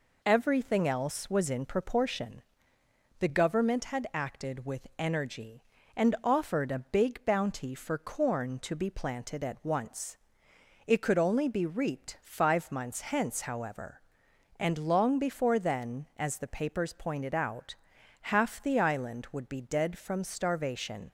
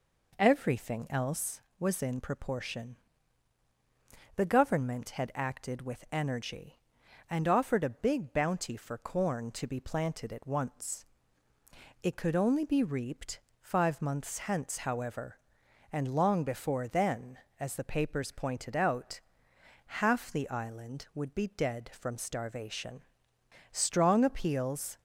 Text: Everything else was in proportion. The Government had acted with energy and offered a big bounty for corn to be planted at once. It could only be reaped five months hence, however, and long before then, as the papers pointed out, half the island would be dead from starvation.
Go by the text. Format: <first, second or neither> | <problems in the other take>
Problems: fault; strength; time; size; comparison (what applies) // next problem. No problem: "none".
first | pauses between "reaped" and "five"; slight; at 13.3 s; 0.22 s long // goes on to say "Strong appeals"; noticeable; from 23.7 s on; 1.2 s long